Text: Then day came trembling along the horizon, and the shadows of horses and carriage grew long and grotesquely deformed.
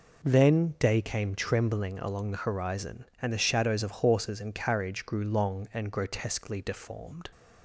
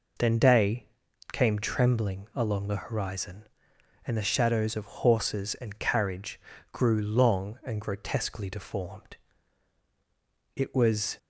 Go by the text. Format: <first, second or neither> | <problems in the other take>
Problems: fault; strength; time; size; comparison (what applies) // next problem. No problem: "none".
first | pauses between "day" and "came"; noticeable; at 0.8 s; 0.46 s long // pauses between "carriage" and "grew"; slight; at 6.3 s; 0.32 s long // goes on to say "It was"; noticeable; from 10.5 s on; 0.62 s long